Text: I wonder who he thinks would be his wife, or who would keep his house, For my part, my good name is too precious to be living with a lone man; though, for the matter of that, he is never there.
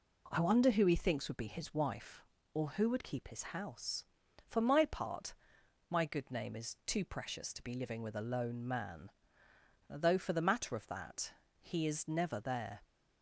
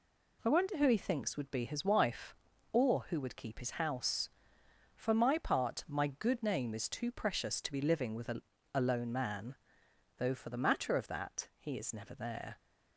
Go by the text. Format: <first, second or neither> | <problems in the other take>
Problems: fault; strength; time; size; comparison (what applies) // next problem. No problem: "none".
first | says "a" twice; at 8.7 s